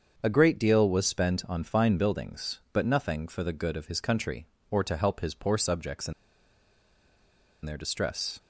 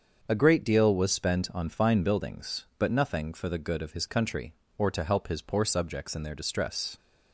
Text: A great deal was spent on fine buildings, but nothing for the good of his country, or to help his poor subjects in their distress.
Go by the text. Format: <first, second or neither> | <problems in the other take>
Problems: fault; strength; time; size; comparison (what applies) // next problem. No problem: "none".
second | starts louder than the rest; until 1.2 s; 7 dB; also in the second // pauses between "in" and "their"; strong; at 6.1 s; 1.5 s long